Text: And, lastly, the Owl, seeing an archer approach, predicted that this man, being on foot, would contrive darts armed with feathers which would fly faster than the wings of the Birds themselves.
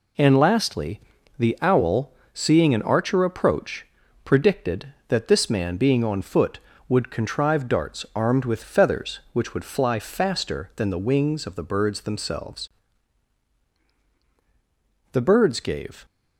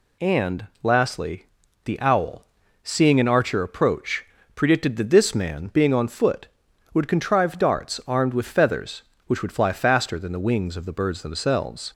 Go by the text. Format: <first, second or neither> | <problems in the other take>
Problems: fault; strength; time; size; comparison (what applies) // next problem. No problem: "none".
second | goes on to say "The Birds gave"; noticeable; from 15.1 s on; 0.92 s long